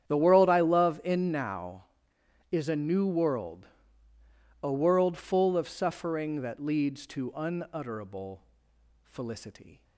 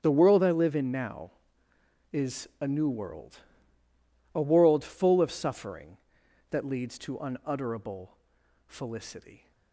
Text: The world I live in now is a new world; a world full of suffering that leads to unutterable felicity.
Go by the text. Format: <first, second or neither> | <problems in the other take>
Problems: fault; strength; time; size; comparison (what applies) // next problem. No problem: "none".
second | starts louder than the rest; strong; until 1.1 s; 9.5 dB; strong in the second // says "love" for "live"; at 0.5 s // pauses between "unutterable" and "felicity"; noticeable; at 8.4 s; 0.64 s long; noticeable in the second